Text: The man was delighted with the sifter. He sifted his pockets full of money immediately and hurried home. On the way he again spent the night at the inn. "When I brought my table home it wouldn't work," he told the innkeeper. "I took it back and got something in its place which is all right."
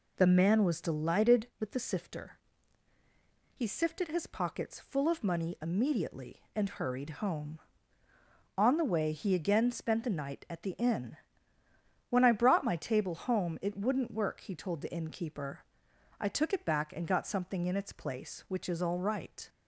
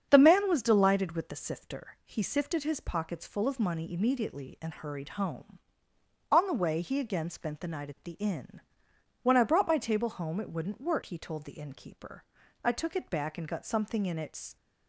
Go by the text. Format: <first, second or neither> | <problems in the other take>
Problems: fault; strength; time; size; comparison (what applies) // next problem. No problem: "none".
first | starts louder than the rest; strong; until 1.1 s; 7.5 dB // stops before "place which is all right"; at 14.5 s